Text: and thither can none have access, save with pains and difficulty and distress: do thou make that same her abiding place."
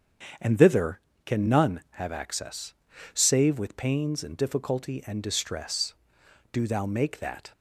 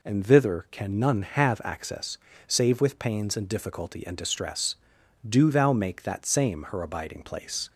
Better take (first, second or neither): second